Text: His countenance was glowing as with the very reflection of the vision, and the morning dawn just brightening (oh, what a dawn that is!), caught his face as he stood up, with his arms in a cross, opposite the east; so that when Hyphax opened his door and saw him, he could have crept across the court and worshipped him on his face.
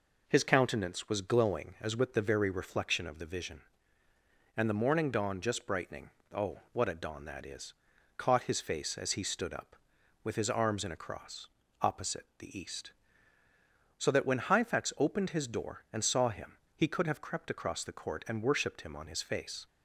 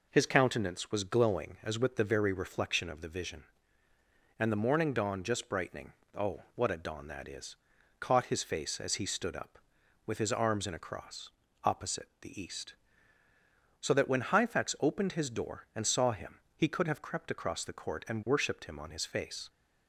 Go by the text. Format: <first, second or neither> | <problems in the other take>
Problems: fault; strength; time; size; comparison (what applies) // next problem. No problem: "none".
neither | none